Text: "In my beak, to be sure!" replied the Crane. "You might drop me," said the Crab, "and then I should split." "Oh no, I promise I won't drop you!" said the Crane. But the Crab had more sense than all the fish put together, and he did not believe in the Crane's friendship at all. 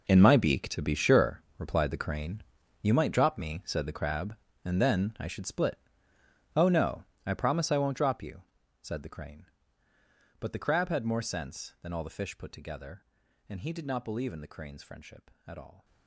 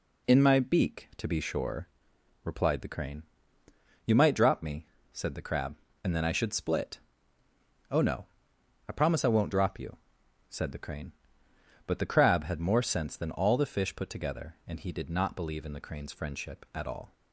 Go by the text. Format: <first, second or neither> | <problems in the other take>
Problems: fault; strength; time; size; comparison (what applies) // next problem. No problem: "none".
second | gets quieter; strong; throughout; 15 dB